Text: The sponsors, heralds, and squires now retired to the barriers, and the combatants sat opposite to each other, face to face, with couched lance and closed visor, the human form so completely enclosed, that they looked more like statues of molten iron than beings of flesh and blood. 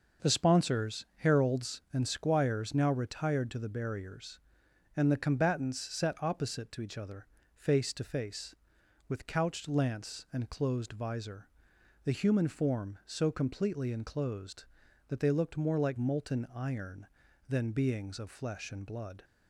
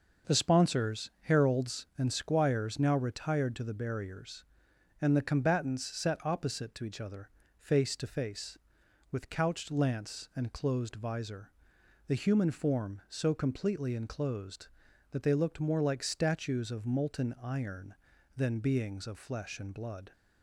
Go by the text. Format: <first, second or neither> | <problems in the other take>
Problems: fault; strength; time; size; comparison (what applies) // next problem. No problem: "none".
second | skips "statues of"; at 15.9 s